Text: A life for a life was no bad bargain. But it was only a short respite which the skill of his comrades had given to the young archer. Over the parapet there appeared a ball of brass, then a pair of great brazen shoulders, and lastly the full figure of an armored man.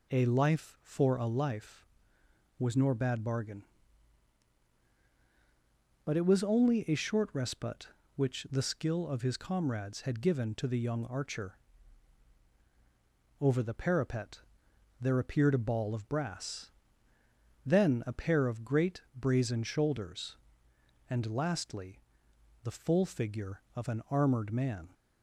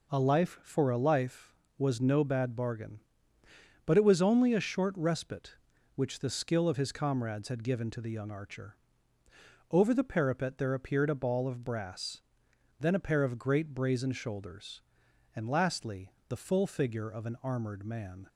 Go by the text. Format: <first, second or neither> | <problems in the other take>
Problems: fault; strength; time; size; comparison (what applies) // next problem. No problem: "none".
second | says "nor" for "no"; at 2.7 s // pauses between "parapet" and "there"; noticeable; at 14.3 s; 0.62 s long // pauses between "lastly" and "the"; noticeable; at 22.0 s; 0.62 s long; slight in the second